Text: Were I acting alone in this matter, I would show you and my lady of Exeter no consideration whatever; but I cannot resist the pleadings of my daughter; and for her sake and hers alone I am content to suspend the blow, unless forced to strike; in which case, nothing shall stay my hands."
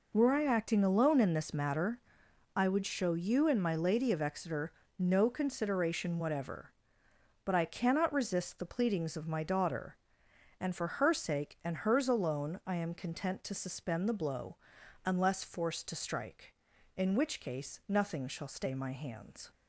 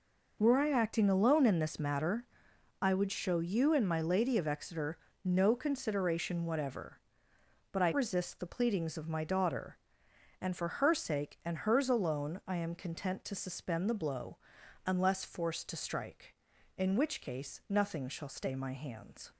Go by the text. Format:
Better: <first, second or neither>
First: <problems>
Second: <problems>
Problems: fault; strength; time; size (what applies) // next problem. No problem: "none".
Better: first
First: pauses between "Exeter" and "no"; slight; at 4.7 s; 0.28 s long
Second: pauses between "Exeter" and "no"; slight; at 4.9 s; 0.28 s long // skips "cannot"; at 7.9 s